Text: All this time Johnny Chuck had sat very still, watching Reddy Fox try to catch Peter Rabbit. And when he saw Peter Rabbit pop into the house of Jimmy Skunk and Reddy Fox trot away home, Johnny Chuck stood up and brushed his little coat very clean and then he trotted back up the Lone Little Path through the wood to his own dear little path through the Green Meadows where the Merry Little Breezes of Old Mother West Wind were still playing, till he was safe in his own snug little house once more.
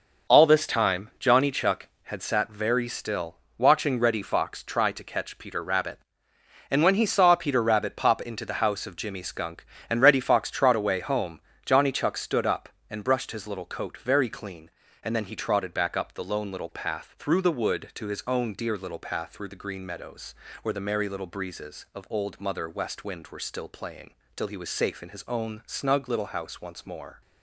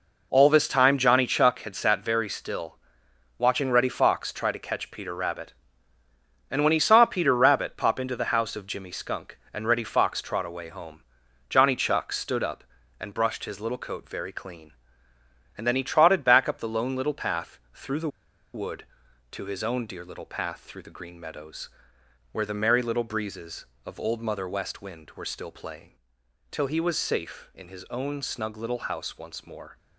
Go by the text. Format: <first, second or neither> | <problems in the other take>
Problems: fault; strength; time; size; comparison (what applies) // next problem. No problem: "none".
first | pauses between "Path" and "through"; slight; at 17.5 s; 0.16 s long // pauses between "the" and "wood"; noticeable; at 18.0 s; 0.46 s long // pauses between "Meadows" and "where"; noticeable; at 21.6 s; 0.62 s long; slight in the first